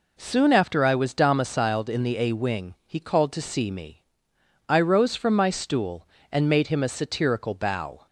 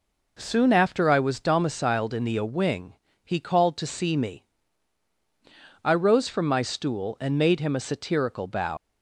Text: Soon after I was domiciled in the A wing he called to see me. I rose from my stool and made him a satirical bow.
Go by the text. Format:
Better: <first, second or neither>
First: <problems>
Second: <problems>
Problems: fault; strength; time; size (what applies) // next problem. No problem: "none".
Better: first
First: none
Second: pauses between "wing" and "he"; slight; at 2.9 s; 0.32 s long // leaves "bow" unfinished; at 8.7 s; 120 ms